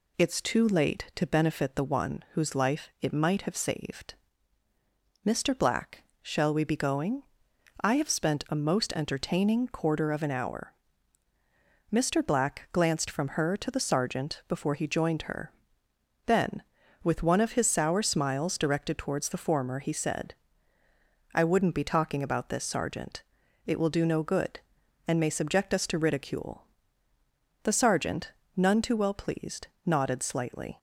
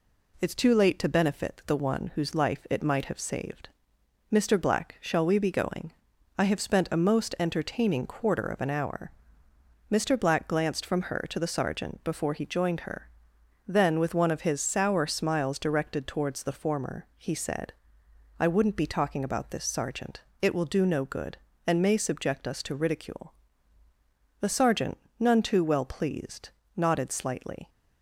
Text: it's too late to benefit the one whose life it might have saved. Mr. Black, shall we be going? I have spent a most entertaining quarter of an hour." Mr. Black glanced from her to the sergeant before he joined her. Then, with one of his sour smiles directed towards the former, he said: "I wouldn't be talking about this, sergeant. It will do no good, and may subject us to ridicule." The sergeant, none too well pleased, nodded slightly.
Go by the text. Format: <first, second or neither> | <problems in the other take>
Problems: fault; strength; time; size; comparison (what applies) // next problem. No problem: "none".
neither | none